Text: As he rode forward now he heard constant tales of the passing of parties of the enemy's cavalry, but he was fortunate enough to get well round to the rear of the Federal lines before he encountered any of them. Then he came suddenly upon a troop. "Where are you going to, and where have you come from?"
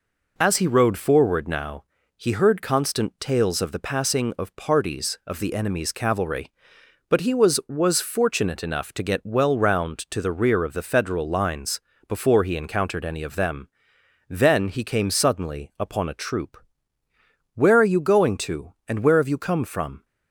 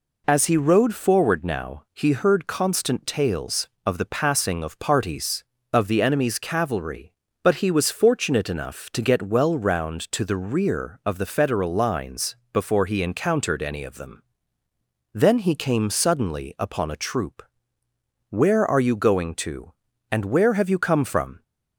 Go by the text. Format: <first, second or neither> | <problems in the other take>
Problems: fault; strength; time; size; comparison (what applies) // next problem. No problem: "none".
second | pauses between "now" and "he"; slight; at 1.8 s; 0.34 s long // says "was" twice; at 7.6 s // pauses between "lines" and "before"; slight; at 11.7 s; 0.28 s long; slight in the second